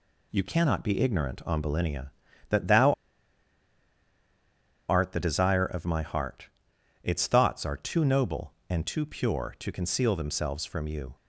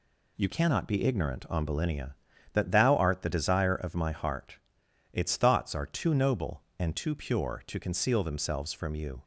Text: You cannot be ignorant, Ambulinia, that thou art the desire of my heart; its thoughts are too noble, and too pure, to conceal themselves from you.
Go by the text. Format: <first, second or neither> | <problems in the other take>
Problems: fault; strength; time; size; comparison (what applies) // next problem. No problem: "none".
second | pauses between "thou" and "art"; strong; at 2.9 s; 1.9 s long